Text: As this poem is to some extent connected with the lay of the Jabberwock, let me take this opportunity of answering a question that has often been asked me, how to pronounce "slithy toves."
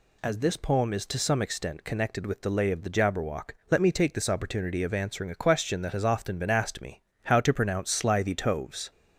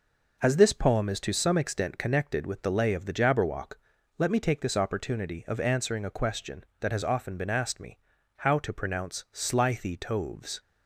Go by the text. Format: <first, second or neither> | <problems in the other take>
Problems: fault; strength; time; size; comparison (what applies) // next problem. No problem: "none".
neither | none